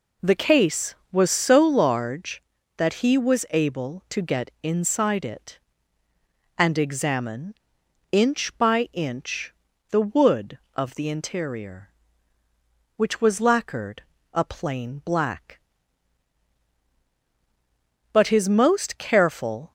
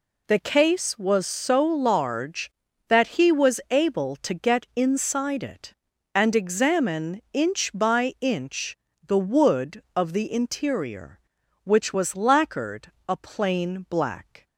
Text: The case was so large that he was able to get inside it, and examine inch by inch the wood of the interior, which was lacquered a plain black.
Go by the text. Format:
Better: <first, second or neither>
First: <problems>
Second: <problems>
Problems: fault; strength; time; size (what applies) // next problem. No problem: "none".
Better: second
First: pauses between "examine" and "inch"; noticeable; at 7.5 s; 0.58 s long // pauses between "inch" and "the"; at 9.5 s; 0.38 s long // pauses between "lacquered" and "a"; slight; at 14.0 s; 0.32 s long // goes on to say "But his most careful"; from 18.1 s on; 1.6 s long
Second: pauses between "inch" and "the"; slight; at 8.7 s; 0.32 s long // pauses between "lacquered" and "a"; slight; at 12.9 s; 0.16 s long